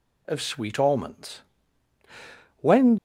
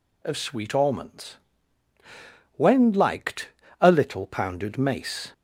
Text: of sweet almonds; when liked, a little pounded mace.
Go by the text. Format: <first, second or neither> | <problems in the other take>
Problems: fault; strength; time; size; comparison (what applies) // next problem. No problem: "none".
second | stops before "liked a little pounded mace"; at 2.9 s